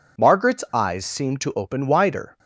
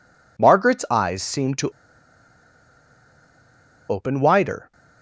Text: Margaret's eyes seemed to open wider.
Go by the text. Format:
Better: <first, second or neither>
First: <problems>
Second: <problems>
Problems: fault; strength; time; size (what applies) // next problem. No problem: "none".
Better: first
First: none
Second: pauses between "to" and "open"; strong; at 1.6 s; 2.1 s long